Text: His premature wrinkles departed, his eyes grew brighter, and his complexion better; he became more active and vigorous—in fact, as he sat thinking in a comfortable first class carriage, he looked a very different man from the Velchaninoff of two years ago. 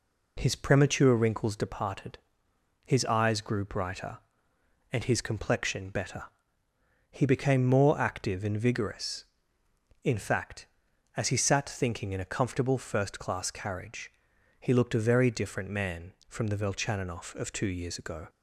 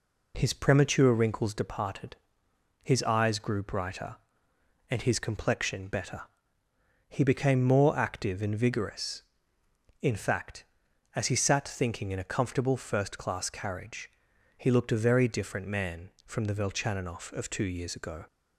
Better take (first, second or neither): neither